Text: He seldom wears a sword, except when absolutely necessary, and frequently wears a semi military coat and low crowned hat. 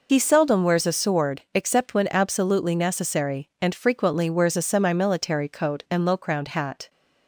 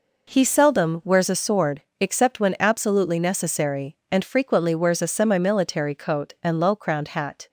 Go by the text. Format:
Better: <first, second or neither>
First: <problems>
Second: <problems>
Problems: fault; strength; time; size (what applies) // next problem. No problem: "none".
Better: second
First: loses the start of "He"; at 0.0 s; 60 ms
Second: none